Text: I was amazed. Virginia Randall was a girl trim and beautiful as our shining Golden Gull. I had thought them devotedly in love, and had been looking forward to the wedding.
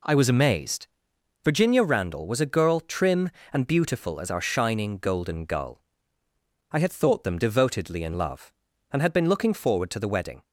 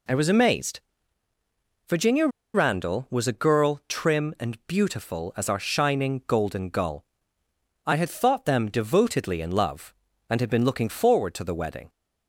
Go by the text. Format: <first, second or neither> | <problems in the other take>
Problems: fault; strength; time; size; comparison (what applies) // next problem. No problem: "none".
first | pauses between "Virginia" and "Randall"; slight; at 2.2 s; 0.28 s long